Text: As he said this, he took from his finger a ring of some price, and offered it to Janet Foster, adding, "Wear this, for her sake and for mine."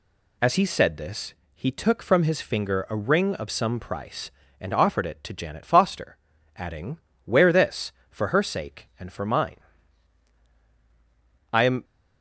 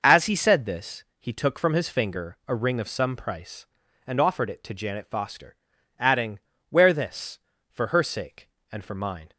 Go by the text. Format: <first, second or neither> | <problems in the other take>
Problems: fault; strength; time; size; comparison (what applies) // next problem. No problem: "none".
second | goes on to say "I am"; slight; from 11.5 s on; 0.32 s long